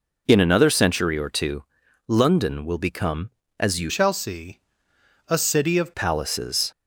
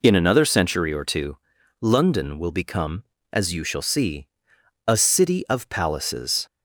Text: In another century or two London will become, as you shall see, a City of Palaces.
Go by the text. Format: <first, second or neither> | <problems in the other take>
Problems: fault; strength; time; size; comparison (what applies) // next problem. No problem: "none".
second | pauses between "two" and "London"; at 1.6 s; 0.44 s long; also in the second // changes voice from "shall" to "of"; from 3.8 to 5.9 s; 2.1 s long